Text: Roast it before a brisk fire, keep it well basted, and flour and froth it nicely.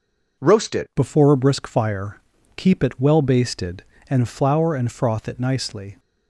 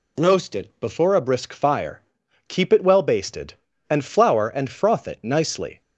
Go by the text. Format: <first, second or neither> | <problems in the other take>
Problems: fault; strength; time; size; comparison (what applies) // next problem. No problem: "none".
second | changes voice at "before"; from 0.9 s on; 5.0 s long